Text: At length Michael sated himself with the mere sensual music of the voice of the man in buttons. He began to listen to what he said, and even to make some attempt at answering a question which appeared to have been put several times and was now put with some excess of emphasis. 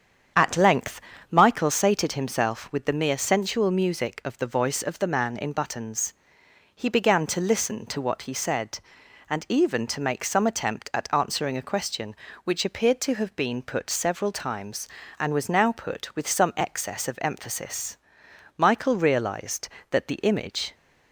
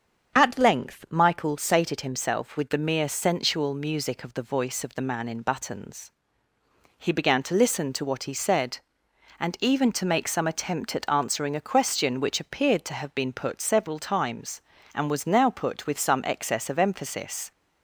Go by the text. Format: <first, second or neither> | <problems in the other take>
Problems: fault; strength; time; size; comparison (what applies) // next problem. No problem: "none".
second | starts louder than the rest; strong; until 1.6 s; 8 dB; strong in the second // pauses between "length" and "Michael"; slight; at 0.9 s; 0.30 s long // goes on to say "Michael realized that the image"; strong; from 18.5 s on; 2.1 s long